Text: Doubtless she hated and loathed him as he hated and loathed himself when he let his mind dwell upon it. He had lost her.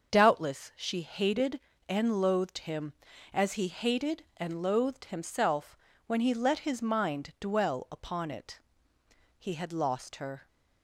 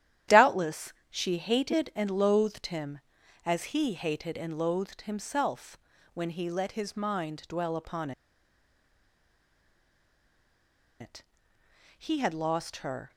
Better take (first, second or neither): first